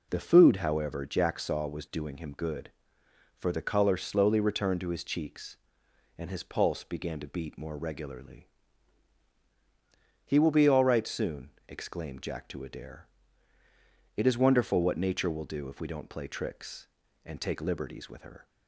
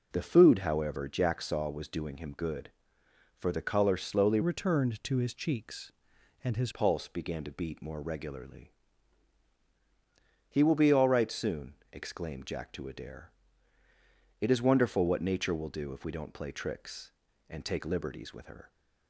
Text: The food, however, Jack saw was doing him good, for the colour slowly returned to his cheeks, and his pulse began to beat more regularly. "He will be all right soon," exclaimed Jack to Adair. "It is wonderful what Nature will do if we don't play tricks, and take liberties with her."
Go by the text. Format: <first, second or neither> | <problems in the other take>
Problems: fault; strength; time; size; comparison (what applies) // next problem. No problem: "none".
first | changes voice from "returned" to "his"; from 4.4 to 6.7 s; 2.3 s long